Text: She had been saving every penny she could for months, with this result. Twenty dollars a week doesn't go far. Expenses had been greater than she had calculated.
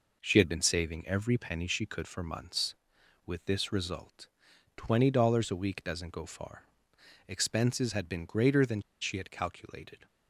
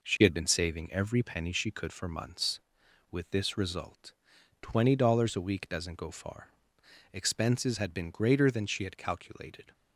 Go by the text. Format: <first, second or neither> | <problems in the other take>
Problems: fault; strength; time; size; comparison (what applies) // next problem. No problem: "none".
second | pauses between "than" and "she"; slight; at 8.8 s; 0.19 s long